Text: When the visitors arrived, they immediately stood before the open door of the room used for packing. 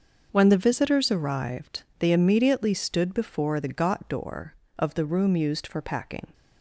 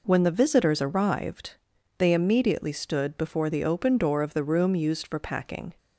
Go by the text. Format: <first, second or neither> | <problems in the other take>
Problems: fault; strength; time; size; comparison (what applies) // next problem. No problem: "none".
second | starts louder than the rest; until 1.3 s; 6 dB // says "got" for "open"; at 3.7 s